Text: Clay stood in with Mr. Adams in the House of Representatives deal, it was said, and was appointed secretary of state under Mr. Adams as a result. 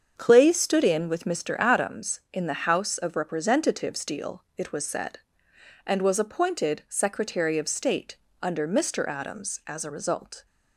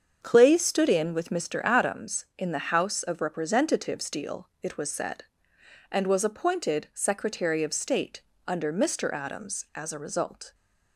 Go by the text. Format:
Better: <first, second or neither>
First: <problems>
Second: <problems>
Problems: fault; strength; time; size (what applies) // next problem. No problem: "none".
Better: neither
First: starts louder than the rest; strong; until 1.1 s; 7 dB // pauses between "state" and "under"; slight; at 8.1 s; 0.26 s long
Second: starts louder than the rest; strong; until 1.2 s; 7 dB // pauses between "state" and "under"; slight; at 8.2 s; 0.26 s long